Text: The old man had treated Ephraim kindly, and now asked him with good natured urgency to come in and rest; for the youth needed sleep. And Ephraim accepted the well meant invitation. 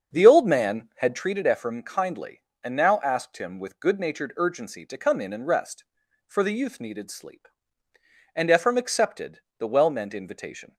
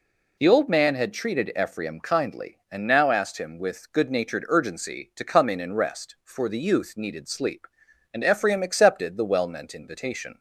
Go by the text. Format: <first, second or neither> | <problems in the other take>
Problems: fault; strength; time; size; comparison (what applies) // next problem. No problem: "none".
second | starts louder than the rest; until 1.3 s; 7 dB // pauses between "accepted" and "the"; slight; at 9.3 s; 0.20 s long